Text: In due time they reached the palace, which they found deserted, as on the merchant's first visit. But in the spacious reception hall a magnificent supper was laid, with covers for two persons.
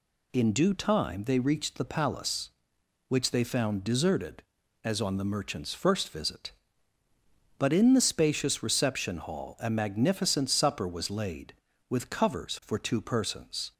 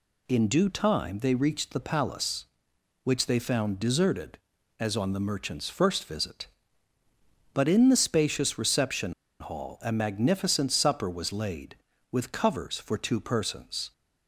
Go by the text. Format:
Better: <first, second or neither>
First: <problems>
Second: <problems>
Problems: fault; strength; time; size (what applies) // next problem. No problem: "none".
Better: first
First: none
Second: pauses between "reception" and "hall"; slight; at 9.1 s; 0.28 s long